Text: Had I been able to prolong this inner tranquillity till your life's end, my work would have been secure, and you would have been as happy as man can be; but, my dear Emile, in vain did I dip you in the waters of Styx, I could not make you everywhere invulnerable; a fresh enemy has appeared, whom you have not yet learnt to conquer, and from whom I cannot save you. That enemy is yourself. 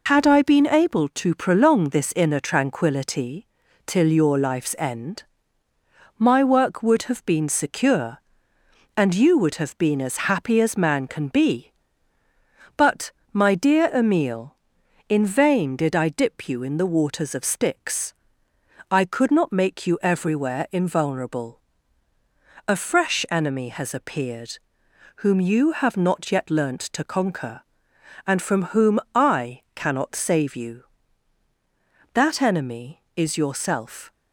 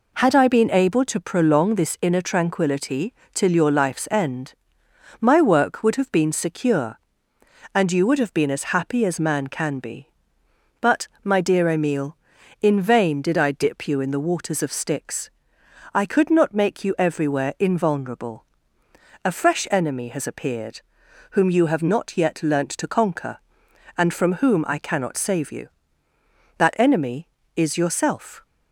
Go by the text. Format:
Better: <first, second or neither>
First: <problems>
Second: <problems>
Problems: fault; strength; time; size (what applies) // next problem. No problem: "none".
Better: second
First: loses the start of "Had"; at 0.0 s; 55 ms // pauses between "tranquillity" and "till"; at 3.4 s; 0.40 s long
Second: pauses between "tranquillity" and "till"; slight; at 3.1 s; 0.20 s long